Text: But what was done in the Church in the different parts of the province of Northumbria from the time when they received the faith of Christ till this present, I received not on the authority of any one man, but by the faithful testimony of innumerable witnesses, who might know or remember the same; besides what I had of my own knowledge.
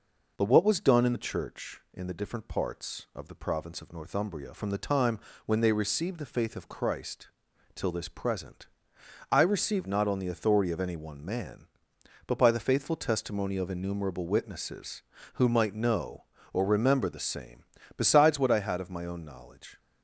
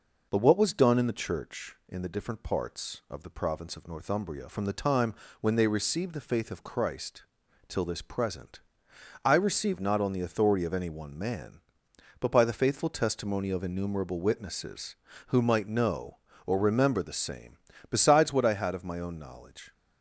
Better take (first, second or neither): neither